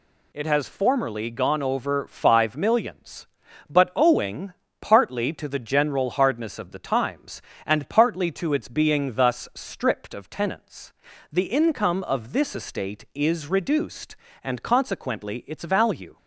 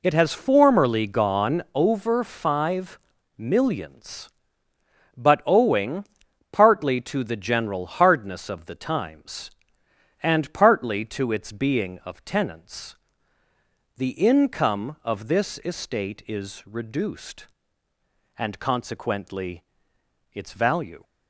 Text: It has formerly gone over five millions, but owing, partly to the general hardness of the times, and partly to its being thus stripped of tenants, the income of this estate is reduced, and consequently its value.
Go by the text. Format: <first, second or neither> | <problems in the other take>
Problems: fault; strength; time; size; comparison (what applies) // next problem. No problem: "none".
first | pauses between "five" and "millions"; at 2.9 s; 0.40 s long // skips "thus stripped"; at 12.0 s // pauses between "consequently" and "its"; noticeable; at 19.6 s; 0.70 s long